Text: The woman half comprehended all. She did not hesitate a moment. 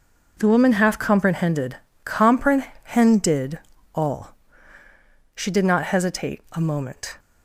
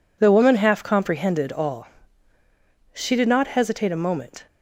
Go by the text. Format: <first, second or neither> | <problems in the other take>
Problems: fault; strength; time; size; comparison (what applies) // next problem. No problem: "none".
second | says "comprehended" twice; at 2.0 s